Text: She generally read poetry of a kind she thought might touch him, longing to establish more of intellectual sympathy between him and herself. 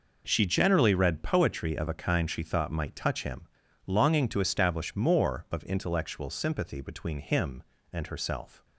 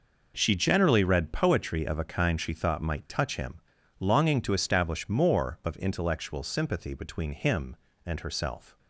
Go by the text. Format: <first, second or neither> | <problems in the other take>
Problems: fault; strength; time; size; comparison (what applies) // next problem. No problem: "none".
neither | none